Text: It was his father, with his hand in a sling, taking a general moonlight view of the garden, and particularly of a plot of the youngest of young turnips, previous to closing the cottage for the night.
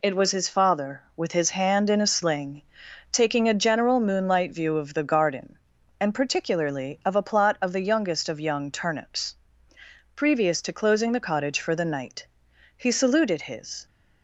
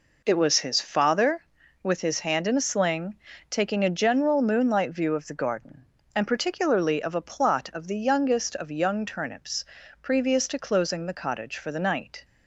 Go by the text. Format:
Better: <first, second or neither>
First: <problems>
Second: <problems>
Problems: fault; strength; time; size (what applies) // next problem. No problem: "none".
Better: second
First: goes on to say "He saluted his"; noticeable; from 12.7 s on; 1.0 s long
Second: none